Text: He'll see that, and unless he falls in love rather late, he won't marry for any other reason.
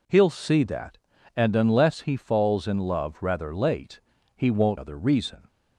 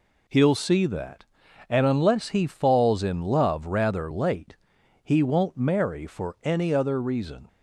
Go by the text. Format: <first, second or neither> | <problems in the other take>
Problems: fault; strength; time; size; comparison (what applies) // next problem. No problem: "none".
second | skips "marry for any"; at 4.7 s